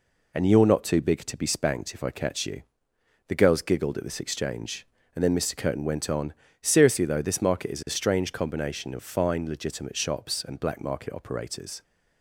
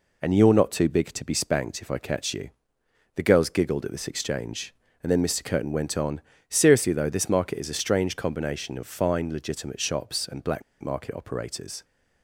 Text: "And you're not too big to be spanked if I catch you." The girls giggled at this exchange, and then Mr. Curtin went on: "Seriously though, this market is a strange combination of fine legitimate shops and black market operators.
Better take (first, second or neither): first